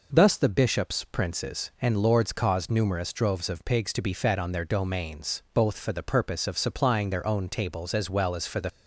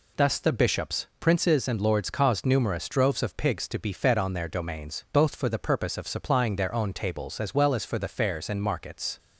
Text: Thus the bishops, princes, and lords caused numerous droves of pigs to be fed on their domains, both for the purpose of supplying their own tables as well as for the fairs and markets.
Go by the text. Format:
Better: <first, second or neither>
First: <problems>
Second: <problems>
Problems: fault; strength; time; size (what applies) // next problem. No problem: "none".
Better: second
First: stops before "fairs and markets"; at 8.6 s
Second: none